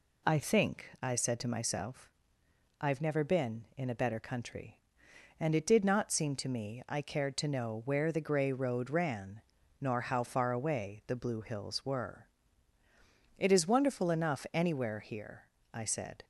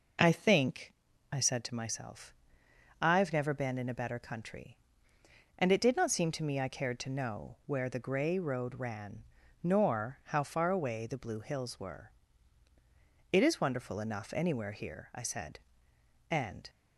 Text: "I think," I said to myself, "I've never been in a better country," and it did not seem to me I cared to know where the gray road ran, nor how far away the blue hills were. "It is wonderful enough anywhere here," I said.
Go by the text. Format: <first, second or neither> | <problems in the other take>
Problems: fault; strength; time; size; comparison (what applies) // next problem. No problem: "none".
first | goes on to say "And"; slight; from 16.2 s on; 0.40 s long